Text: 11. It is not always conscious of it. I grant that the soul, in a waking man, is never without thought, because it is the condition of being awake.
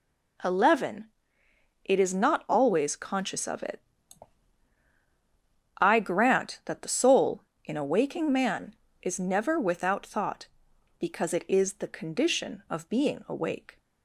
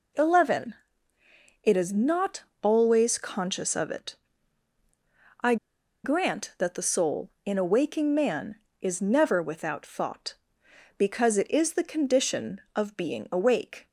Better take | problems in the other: first | pauses between "not" and "always"; slight; at 2.4 s; 0.18 s long // pauses between "I" and "grant"; noticeable; at 5.5 s; 0.48 s long

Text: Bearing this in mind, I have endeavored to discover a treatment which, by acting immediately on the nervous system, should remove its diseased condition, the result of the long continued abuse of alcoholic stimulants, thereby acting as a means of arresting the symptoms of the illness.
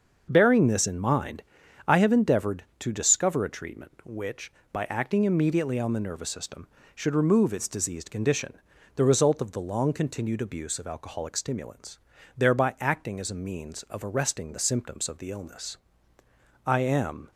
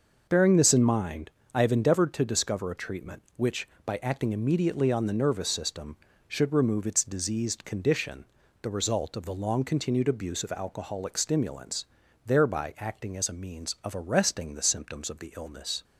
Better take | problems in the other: second | goes on to say "I am"; noticeable; from 16.6 s on; 0.64 s long

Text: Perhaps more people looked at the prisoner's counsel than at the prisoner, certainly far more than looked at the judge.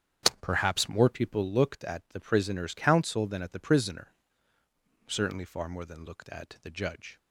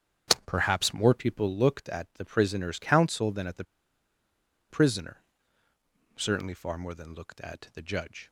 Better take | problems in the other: first | starts louder than the rest; strong; until 1.4 s; 7 dB; also in the first // pauses between "the" and "prisoner"; at 3.6 s; 1.0 s long

